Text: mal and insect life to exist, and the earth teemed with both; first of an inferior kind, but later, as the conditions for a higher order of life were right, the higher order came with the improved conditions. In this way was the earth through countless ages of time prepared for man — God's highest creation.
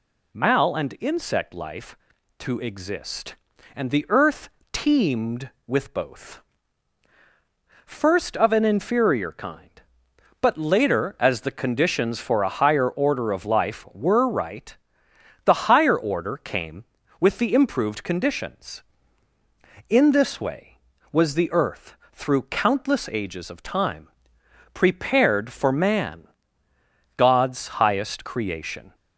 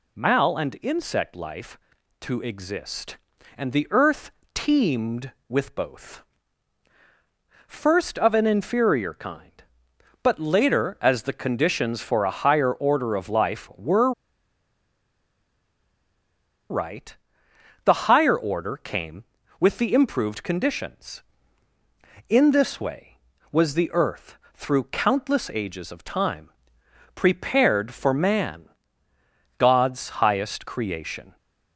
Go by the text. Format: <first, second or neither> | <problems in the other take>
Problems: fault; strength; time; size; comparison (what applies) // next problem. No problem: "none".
first | pauses between "earth" and "teemed"; slight; at 4.2 s; 0.24 s long; slight in the first // pauses between "were" and "right"; strong; at 14.1 s; 2.5 s long // pauses between "earth" and "through"; slight; at 24.3 s; 0.18 s long; slight in the first // pauses between "time" and "prepared"; noticeable; at 26.4 s; 0.64 s long; noticeable in the first